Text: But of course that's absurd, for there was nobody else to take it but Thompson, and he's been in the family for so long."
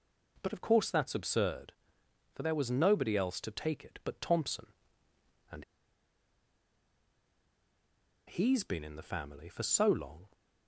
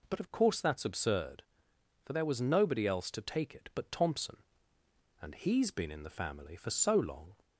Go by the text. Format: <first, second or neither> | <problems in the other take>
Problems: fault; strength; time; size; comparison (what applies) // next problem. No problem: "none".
second | pauses between "and" and "he's"; strong; at 5.6 s; 2.6 s long